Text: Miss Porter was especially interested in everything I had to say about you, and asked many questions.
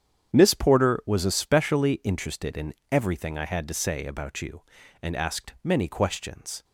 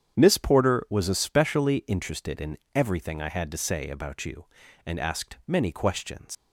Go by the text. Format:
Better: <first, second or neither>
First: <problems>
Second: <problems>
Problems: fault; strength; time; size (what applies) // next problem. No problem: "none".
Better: first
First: starts louder than the rest; strong; until 1.3 s; 8.5 dB // pauses between "in" and "everything"; slight; at 2.7 s; 0.16 s long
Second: starts louder than the rest; strong; until 1.2 s; 8.5 dB // pauses between "in" and "everything"; slight; at 2.5 s; 0.16 s long // leaves "questions" unfinished; at 6.3 s; 120 ms